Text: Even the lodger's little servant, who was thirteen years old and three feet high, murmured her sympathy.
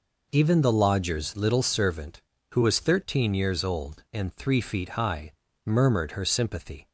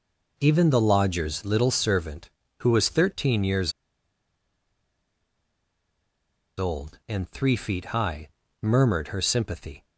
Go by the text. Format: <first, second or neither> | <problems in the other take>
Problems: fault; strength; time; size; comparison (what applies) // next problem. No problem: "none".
first | pauses between "years" and "old"; strong; at 3.7 s; 2.8 s long